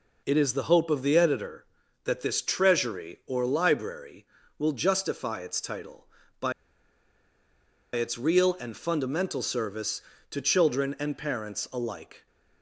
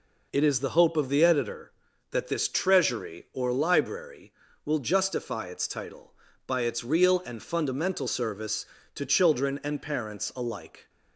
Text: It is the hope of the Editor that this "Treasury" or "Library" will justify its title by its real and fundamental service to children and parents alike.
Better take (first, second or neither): second